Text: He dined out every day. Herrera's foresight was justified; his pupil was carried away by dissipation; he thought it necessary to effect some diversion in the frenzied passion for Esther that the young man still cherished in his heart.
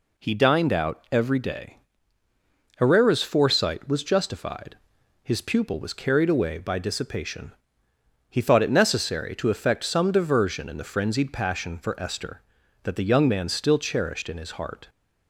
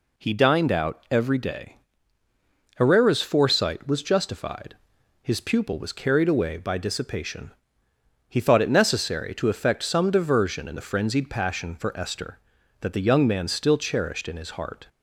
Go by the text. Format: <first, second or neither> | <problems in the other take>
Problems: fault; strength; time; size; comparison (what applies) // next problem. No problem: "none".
neither | none